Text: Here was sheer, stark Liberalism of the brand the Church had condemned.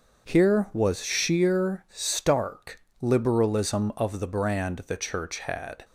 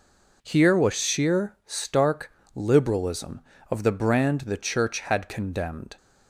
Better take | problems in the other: second | starts louder than the rest; noticeable; until 1.3 s; 6 dB // pauses between "stark" and "Liberalism"; slight; at 2.8 s; 0.20 s long; slight in the second // stops before "condemned"; at 5.8 s

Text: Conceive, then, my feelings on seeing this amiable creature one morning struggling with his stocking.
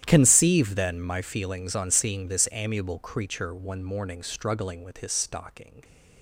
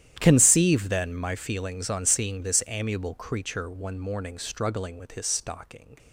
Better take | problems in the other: neither | starts louder than the rest; strong; the same in both

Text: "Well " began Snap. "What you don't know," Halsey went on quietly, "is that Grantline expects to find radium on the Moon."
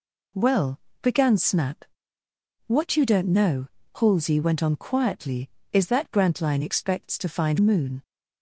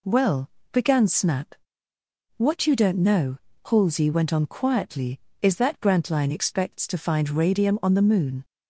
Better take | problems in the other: second | skips "radium on the"; at 7.5 s

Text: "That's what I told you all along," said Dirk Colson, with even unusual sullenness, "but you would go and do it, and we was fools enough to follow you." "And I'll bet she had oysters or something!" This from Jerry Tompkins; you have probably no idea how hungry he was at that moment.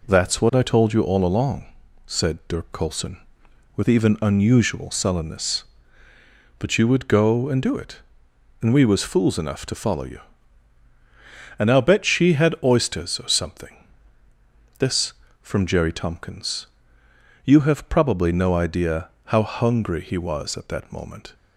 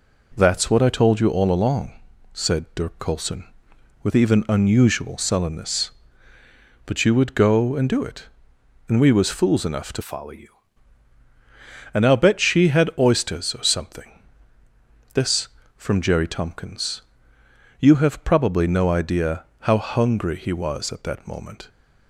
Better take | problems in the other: first | changes voice from "follow" to "you"; from 10.0 to 10.5 s; 0.5 s long // pauses between "idea" and "how"; slight; at 19.4 s; 0.18 s long; slight in the first

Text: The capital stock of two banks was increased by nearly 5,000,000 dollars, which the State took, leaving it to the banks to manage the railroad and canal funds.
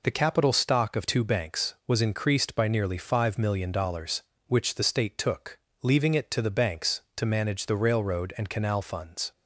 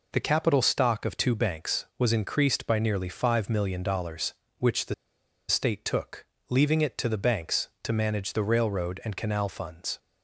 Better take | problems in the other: first | pauses between "the" and "State"; noticeable; at 4.9 s; 0.55 s long

